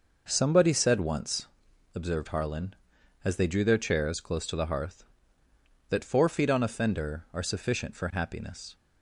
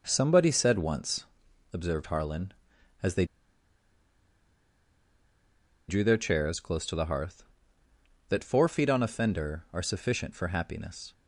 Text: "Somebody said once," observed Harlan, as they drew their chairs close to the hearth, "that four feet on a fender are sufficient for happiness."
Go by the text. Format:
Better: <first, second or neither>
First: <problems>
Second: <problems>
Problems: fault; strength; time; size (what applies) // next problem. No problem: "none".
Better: first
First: none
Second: pauses between "they" and "drew"; strong; at 3.2 s; 2.6 s long